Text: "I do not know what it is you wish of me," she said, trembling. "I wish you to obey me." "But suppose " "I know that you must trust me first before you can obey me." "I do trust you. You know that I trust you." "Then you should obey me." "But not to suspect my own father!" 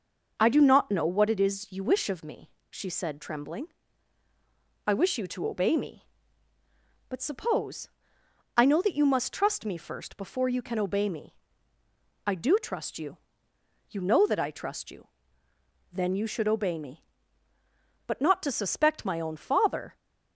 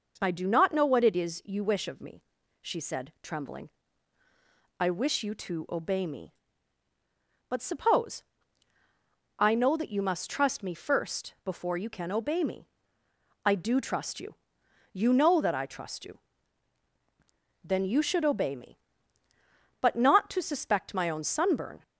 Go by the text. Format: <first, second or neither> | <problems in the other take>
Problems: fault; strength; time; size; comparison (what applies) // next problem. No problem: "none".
first | says "sunburn" for "father"; at 21.2 s